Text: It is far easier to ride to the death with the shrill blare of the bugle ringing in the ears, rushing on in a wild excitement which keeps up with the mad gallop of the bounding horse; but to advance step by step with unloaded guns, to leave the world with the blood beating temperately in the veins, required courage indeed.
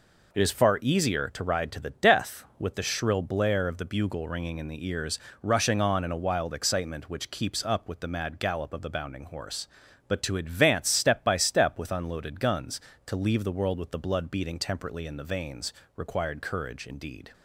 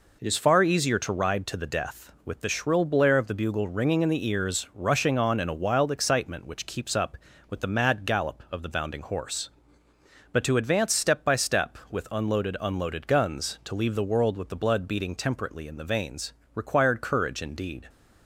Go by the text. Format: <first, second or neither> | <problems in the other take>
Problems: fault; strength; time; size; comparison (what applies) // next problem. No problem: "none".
first | says "unloaded" twice; at 12.6 s